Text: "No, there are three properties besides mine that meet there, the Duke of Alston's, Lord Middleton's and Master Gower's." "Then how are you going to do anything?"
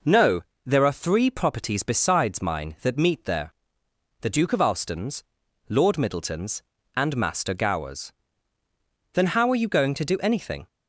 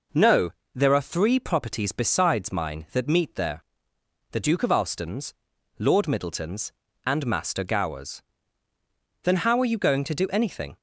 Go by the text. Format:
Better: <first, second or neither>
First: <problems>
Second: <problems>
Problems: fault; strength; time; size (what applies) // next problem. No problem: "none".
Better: neither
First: none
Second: none